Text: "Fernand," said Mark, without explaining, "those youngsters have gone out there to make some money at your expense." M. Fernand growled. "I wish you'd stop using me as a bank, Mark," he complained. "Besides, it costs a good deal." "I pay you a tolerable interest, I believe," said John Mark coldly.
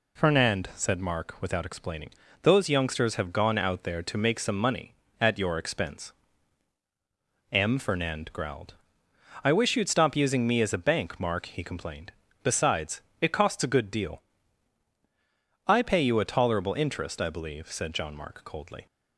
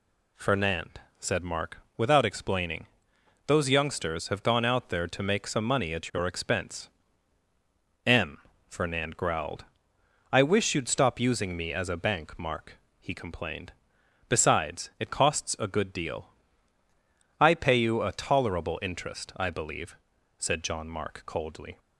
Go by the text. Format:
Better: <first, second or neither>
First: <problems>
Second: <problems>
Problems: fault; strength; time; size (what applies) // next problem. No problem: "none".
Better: neither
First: none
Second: none